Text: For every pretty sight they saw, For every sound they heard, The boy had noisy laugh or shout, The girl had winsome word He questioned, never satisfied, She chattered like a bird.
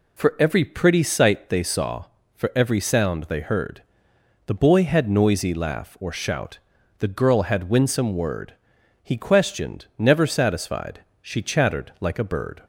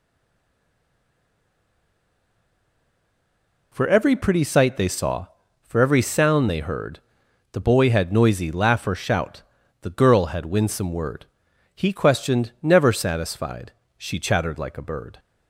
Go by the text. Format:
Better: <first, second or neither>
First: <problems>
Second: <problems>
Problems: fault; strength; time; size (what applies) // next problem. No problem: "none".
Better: first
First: pauses between "word" and "He"; noticeable; at 8.5 s; 0.50 s long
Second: stays silent before the first word; strong; until 3.7 s; 3.7 s long // pauses between "word" and "He"; noticeable; at 11.2 s; 0.48 s long